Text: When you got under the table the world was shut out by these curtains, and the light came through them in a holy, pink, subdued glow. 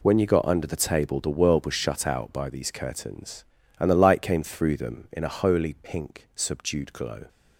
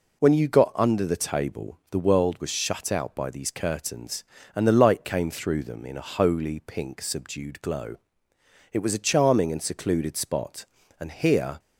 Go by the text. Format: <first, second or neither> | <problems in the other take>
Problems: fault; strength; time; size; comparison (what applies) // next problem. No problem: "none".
first | goes on to say "It was a charming and secluded spot and here"; strong; from 8.7 s on; 2.8 s long